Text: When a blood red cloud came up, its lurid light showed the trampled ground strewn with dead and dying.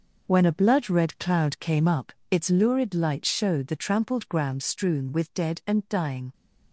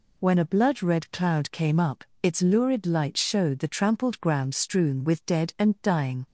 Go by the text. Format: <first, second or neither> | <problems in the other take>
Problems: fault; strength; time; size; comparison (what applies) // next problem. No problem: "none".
second | gets quieter; strong; throughout; 7 dB